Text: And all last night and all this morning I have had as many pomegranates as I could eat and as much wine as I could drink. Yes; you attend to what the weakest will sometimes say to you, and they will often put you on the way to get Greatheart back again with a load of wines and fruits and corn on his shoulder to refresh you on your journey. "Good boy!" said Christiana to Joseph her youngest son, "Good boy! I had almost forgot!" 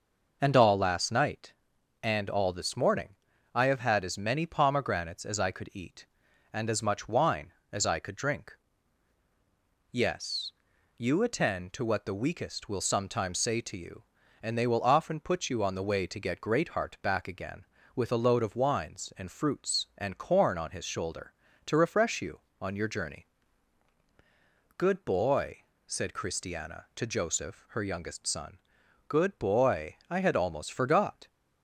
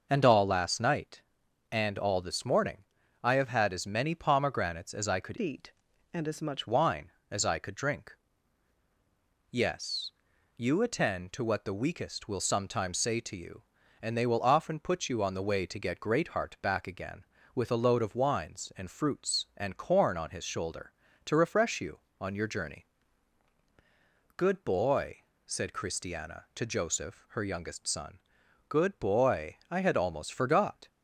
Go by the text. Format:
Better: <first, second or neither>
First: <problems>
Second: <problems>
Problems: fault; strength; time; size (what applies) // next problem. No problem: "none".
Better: first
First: pauses between "morning" and "I"; at 3.1 s; 0.38 s long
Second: pauses between "morning" and "I"; at 2.8 s; 0.38 s long // changes voice from "eat" to "much"; from 5.4 to 6.6 s; 1.2 s long